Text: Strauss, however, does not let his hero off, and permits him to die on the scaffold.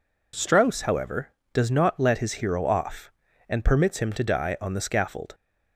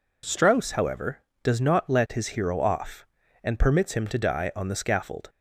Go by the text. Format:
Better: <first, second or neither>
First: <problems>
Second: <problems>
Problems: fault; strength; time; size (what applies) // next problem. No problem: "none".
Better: neither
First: none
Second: none